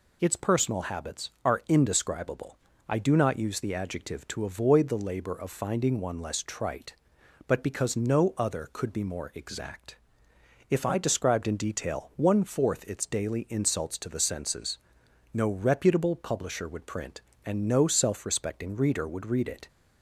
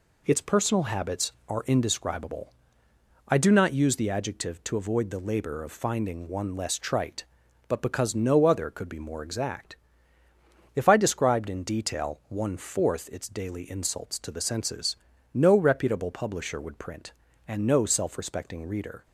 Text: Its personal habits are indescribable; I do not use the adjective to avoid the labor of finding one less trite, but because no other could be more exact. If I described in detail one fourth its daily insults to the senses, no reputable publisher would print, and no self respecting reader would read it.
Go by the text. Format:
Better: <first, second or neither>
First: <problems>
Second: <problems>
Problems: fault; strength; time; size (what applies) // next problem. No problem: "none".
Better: first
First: none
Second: stops before "would read it"; at 19.0 s